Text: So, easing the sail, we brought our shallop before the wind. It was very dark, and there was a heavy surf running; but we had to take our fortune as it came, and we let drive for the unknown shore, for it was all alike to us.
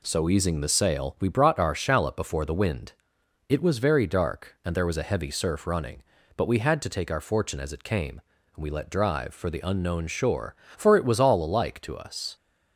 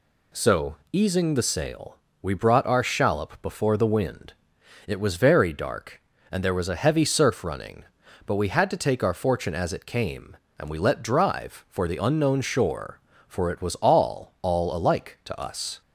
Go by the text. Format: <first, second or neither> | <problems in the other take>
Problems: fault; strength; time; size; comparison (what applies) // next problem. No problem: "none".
first | says "all" twice; at 14.4 s